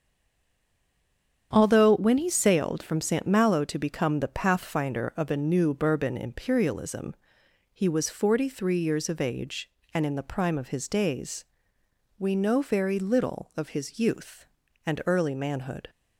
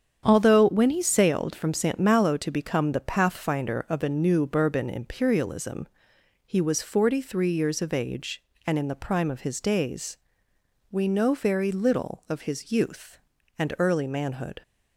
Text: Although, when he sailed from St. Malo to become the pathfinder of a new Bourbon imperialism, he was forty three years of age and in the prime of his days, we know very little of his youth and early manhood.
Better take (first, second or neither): second